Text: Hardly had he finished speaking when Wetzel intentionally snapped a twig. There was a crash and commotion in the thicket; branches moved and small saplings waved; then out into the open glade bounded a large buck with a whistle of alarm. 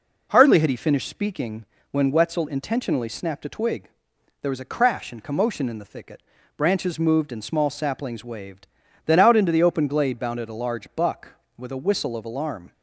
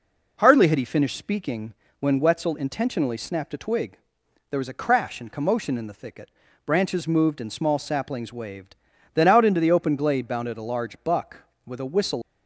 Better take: first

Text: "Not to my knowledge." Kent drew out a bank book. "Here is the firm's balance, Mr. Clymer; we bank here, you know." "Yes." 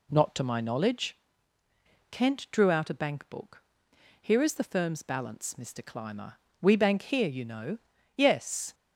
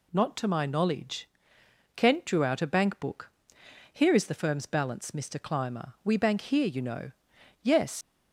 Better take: first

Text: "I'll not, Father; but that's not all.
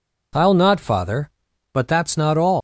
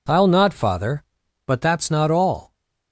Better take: second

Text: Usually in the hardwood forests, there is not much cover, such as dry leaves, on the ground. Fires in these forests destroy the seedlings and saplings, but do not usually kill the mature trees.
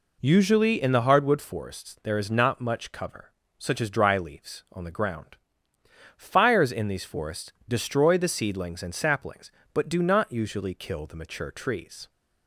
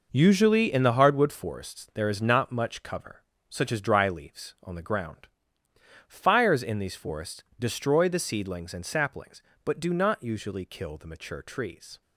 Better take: first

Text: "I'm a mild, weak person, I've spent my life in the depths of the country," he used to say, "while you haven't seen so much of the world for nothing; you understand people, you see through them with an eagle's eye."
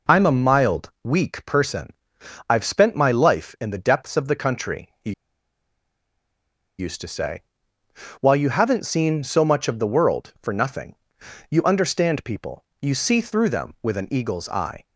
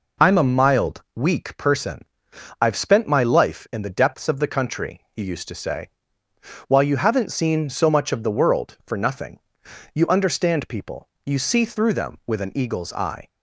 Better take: second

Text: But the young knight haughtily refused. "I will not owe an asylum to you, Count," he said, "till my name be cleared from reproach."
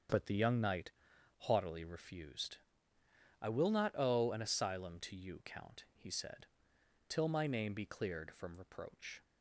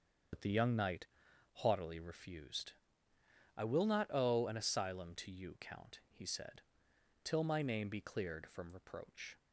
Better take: first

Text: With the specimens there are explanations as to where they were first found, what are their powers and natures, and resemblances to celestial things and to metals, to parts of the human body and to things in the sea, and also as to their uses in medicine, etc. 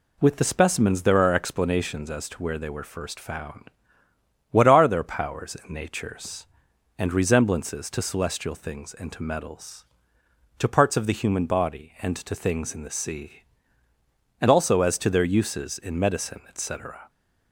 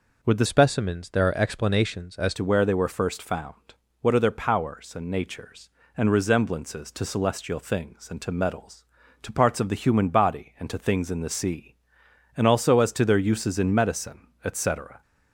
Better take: first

